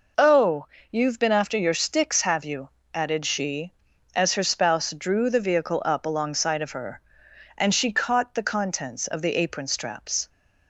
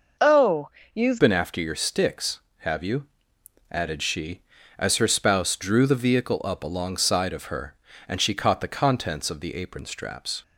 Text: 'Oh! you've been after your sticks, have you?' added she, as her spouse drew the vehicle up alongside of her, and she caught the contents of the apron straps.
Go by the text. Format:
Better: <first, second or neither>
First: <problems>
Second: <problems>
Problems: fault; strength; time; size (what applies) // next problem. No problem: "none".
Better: first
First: none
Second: changes voice at "been"; from 1.2 s on; 9.2 s long